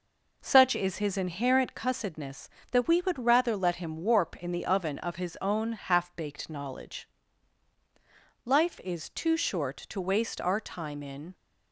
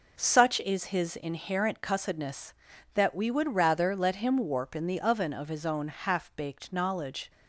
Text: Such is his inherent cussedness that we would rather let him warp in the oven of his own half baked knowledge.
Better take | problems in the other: second | goes on to say "Life is too short to waste our time in"; strong; from 8.4 s on; 2.8 s long

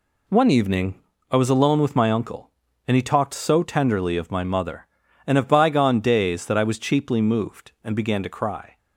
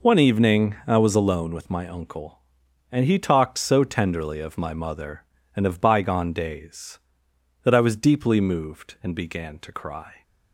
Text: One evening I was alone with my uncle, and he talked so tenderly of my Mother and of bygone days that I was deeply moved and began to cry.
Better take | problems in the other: second | pauses between "evening" and "I"; slight; at 0.9 s; 0.32 s long // says "cheaply" for "deeply"; at 6.7 s

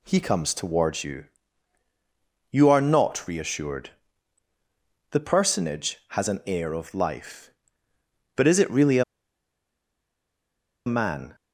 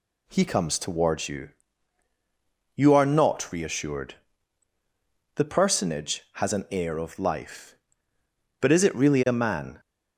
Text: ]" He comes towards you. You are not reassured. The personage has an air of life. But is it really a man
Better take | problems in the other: second | pauses between "a" and "man"; strong; at 9.0 s; 1.8 s long

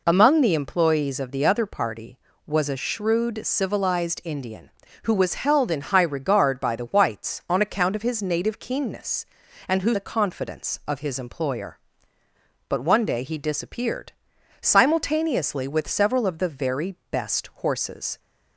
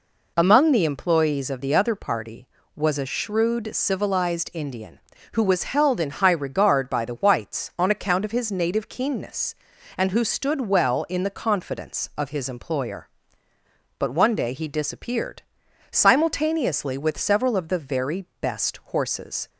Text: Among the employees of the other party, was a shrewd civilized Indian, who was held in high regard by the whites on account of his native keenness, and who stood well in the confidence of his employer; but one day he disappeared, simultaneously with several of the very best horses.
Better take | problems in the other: second | skips "stood well in"; at 9.9 s // pauses between "very" and "best"; slight; at 16.9 s; 0.16 s long; slight in the second

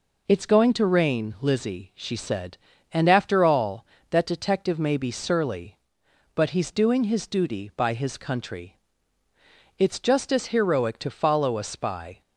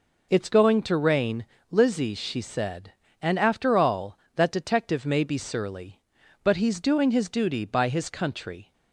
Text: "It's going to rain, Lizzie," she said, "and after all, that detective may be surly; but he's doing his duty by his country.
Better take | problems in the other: second | goes on to say "It's just as heroic to follow a spy"; strong; from 9.7 s on; 2.4 s long

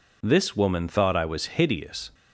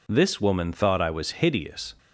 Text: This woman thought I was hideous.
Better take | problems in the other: neither | none

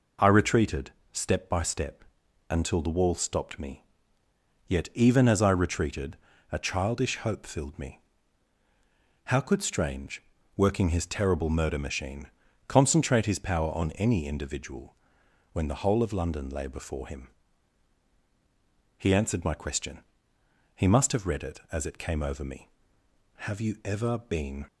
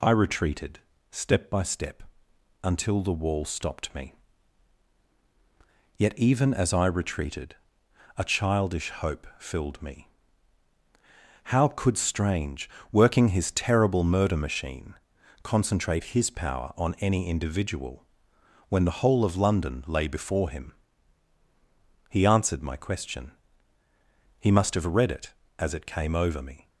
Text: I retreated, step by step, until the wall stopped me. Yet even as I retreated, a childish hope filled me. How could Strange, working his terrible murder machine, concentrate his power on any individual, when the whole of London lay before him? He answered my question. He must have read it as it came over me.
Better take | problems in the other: second | goes on to say "Have you ever been"; noticeable; from 23.3 s on; 1.2 s long

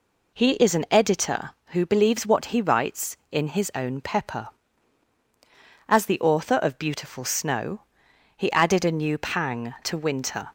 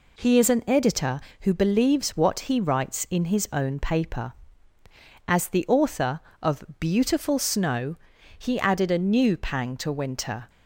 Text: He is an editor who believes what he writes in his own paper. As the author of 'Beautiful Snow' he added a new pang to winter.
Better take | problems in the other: second | says "pepper" for "paper"; at 4.0 s // pauses between "Snow" and "he"; noticeable; at 7.8 s; 0.54 s long; also in the second

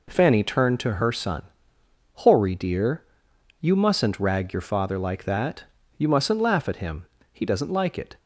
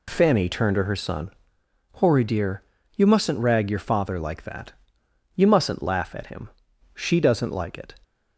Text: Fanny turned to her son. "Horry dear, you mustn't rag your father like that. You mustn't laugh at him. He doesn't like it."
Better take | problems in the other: first | says "She" for "He"; at 6.9 s

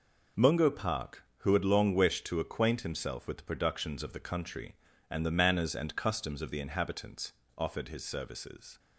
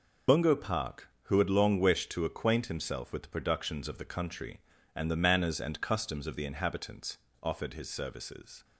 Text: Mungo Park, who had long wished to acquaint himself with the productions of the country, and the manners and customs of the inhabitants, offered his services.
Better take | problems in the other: first | loses the start of "Mungo"; at 0.2 s; 65 ms

